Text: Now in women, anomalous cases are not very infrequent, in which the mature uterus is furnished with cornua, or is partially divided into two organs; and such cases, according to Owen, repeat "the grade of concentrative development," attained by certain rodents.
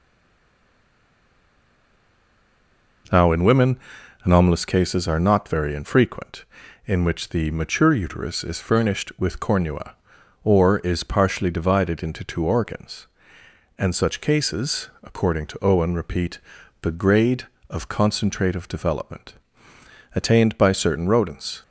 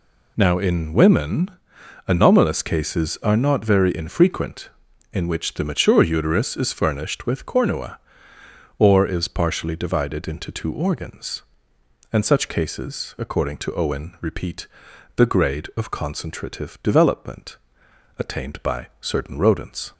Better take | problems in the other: second | stays silent before the first word; strong; until 3.0 s; 3.0 s long // pauses between "repeat" and "the"; at 16.4 s; 0.42 s long; noticeable in the second

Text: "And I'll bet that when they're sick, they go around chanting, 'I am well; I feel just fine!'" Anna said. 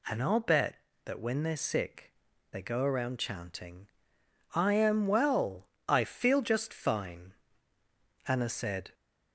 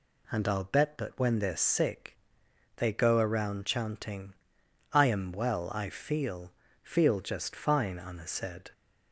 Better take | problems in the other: first | says "feel" twice; at 6.8 s

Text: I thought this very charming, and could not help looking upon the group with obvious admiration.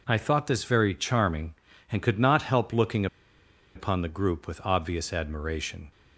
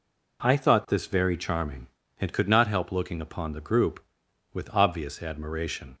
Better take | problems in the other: second | pauses between "looking" and "upon"; noticeable; at 3.0 s; 0.69 s long

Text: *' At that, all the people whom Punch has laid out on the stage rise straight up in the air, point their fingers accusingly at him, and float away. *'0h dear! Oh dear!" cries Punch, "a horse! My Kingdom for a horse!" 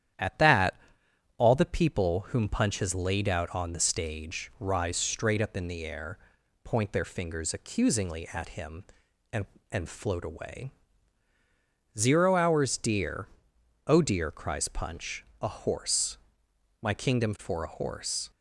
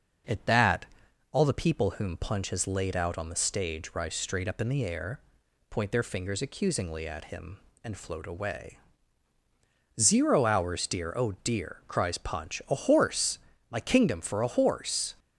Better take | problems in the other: second | starts louder than the rest; strong; until 1.7 s; 10 dB; noticeable in the second // says "and" twice; at 9.7 s

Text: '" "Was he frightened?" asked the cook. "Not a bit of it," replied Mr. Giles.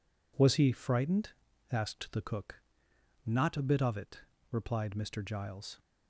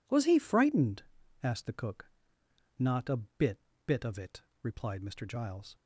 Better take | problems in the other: first | says "bit" twice; at 3.8 s

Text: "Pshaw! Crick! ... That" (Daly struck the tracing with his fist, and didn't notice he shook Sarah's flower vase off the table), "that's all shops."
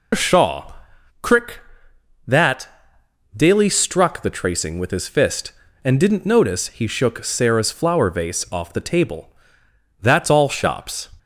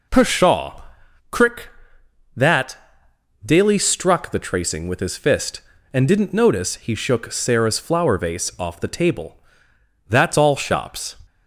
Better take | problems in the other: second | loses the start of "Pshaw"; at 0.1 s; 110 ms

